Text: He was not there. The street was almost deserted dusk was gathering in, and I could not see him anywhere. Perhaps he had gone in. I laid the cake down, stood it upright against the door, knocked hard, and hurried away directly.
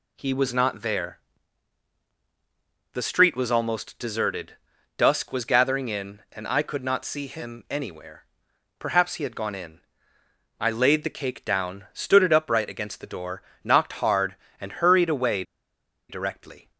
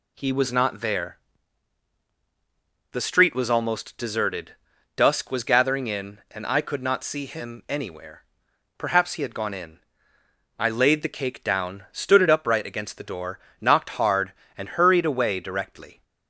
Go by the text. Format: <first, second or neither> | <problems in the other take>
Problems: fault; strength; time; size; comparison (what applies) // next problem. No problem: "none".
second | pauses between "deserted" and "dusk"; at 4.5 s; 0.44 s long; also in the second // pauses between "away" and "directly"; noticeable; at 15.4 s; 0.66 s long